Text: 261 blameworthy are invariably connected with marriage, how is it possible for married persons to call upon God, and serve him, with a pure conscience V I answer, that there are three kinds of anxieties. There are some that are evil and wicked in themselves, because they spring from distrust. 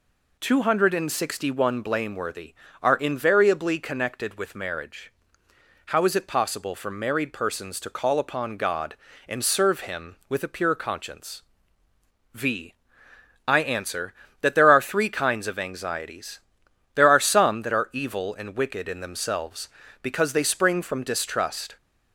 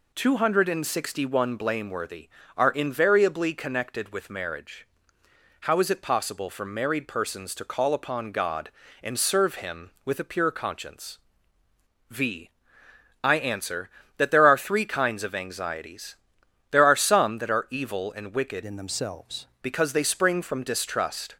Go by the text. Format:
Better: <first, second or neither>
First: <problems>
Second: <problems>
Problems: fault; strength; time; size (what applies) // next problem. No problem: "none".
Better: first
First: pauses between "conscience" and "V"; noticeable; at 11.3 s; 0.94 s long // pauses between "V" and "I"; noticeable; at 12.7 s; 0.74 s long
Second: pauses between "conscience" and "V"; noticeable; at 11.1 s; 0.94 s long // pauses between "V" and "I"; noticeable; at 12.5 s; 0.74 s long // changes voice from "in" to "themselves"; from 18.6 to 19.4 s; 0.8 s long